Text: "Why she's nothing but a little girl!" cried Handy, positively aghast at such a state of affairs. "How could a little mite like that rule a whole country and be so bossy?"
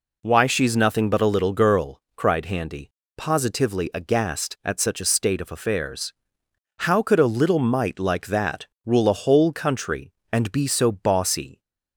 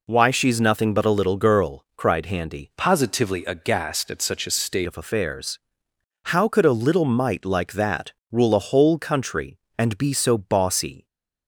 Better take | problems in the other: first | changes voice from "positively" to "state"; from 2.7 to 4.8 s; 2.1 s long // pauses between "that" and "rule"; slight; at 8.1 s; 0.18 s long; slight in the first

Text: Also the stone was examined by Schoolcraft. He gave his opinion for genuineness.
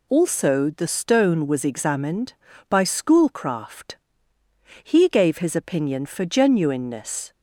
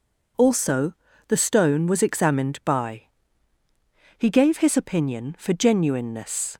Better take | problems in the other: first | pauses between "Also" and "the"; slight; at 0.9 s; 0.36 s long // skips "Schoolcraft"; at 3.6 s

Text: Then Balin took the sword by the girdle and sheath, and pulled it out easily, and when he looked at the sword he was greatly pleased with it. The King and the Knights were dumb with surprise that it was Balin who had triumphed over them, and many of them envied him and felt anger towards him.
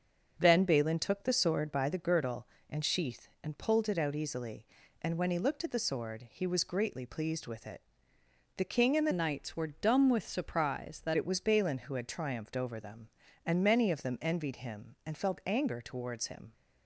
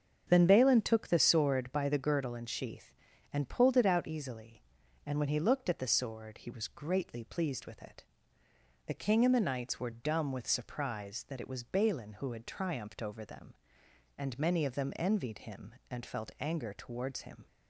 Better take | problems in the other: second | starts louder than the rest; until 1.4 s; 7 dB; strong in the second // changes voice from "Knights" to "that"; from 9.1 to 11.1 s; 2.0 s long

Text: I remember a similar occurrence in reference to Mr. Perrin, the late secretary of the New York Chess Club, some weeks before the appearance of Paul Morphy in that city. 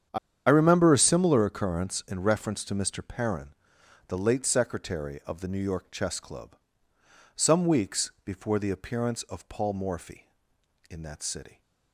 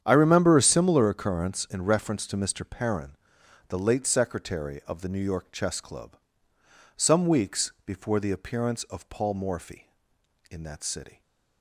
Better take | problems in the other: second | starts louder than the rest; strong; until 1.4 s; 8 dB; strong in the second // pauses between "I" and "remember"; slight; at 0.1 s; 0.30 s long

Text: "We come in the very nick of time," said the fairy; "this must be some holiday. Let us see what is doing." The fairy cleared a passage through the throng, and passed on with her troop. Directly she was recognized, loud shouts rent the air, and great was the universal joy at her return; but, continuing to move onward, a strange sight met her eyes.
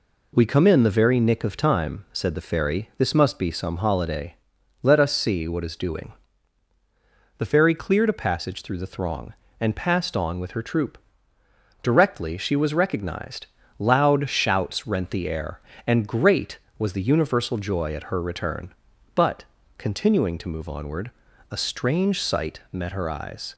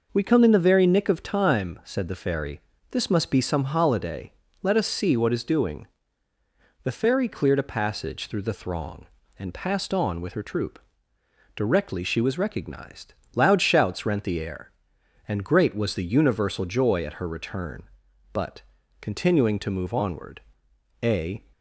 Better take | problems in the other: first | stops before "strange sight met her eyes"; at 21.5 s

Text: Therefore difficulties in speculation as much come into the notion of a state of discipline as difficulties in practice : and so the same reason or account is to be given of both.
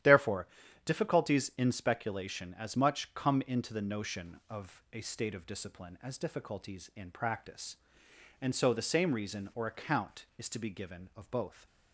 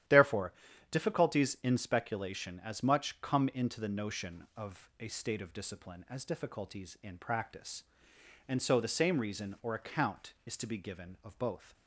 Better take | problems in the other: neither | starts louder than the rest; strong; the same in both // pauses between "Therefore" and "difficulties"; the same in both

